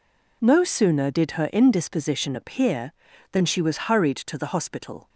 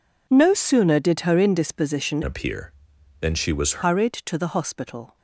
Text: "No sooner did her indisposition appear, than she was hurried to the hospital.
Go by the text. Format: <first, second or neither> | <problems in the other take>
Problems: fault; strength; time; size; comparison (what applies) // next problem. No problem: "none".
first | changes voice from "appear" to "was"; from 2.2 to 3.8 s; 1.6 s long